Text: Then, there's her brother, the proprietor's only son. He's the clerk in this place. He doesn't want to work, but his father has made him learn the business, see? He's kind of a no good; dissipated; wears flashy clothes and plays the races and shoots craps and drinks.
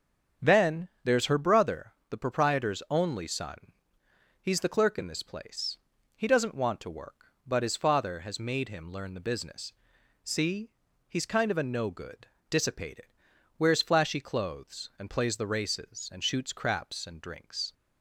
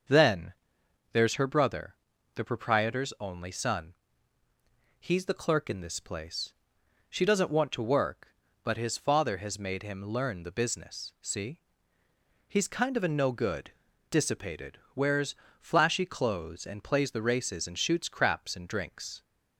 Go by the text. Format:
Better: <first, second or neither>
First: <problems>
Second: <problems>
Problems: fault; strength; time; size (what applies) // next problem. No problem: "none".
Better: first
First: starts louder than the rest; strong; until 1.5 s; 7 dB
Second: starts louder than the rest; until 1.6 s; 6.5 dB // says "She" for "He"; at 7.0 s // pauses between "wears" and "flashy"; slight; at 15.3 s; 0.24 s long